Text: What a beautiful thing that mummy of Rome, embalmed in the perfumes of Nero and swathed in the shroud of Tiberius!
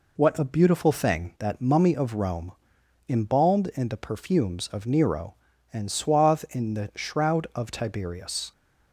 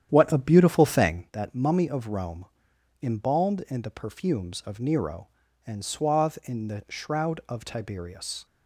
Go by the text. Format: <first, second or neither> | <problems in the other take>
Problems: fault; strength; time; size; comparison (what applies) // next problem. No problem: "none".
first | starts louder than the rest; strong; until 1.2 s; 10 dB